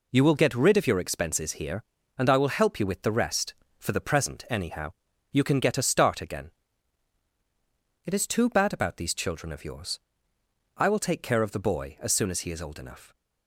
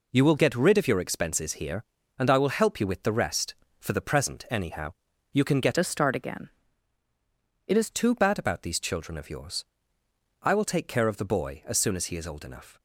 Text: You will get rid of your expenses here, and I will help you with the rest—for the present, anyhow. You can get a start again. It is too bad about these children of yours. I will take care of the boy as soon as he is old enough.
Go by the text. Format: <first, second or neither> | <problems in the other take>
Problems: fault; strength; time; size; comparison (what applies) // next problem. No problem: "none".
first | changes voice from "a" to "is"; from 5.7 to 7.9 s; 2.2 s long